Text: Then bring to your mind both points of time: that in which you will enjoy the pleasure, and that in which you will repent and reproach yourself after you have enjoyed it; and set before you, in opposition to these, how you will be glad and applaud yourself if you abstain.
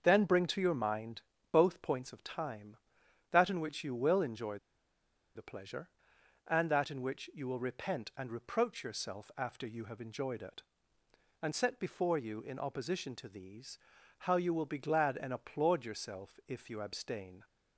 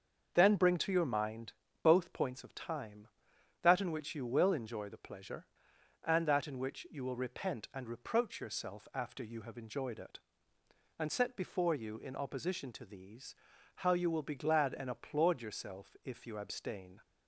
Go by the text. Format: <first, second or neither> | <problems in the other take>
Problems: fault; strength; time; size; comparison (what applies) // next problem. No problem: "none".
second | starts louder than the rest; until 1.0 s; 6.5 dB; also in the second // pauses between "mind" and "both"; slight; at 1.2 s; 0.30 s long; slight in the second // pauses between "enjoy" and "the"; noticeable; at 4.5 s; 0.78 s long